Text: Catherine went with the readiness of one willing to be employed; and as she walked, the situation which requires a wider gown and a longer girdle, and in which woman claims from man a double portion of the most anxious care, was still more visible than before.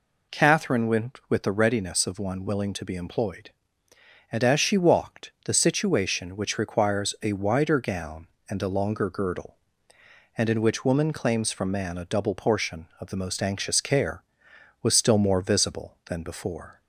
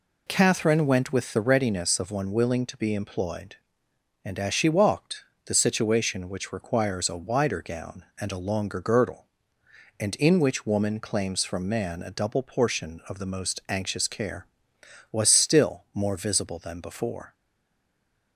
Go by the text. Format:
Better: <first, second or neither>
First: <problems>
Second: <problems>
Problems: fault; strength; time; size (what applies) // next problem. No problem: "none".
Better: first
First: none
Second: stays silent after the last word; from 17.3 s on; 1.0 s long